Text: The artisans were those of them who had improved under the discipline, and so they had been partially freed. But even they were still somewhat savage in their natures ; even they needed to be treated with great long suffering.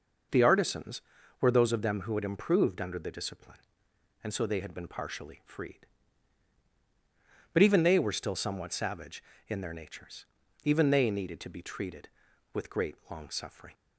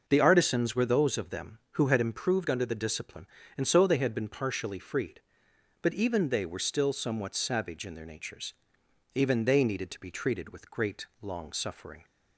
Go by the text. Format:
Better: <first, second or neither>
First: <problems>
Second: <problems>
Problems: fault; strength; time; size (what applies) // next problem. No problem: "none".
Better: neither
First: none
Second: none